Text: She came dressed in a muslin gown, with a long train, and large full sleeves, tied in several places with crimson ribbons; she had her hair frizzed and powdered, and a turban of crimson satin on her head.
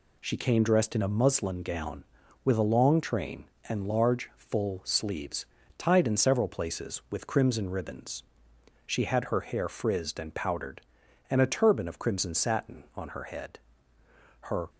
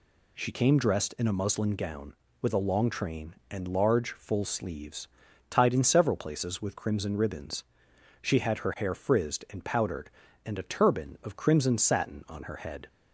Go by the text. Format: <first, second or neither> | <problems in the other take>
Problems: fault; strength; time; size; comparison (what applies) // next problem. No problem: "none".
second | goes on to say "Her"; slight; from 14.4 s on; 0.28 s long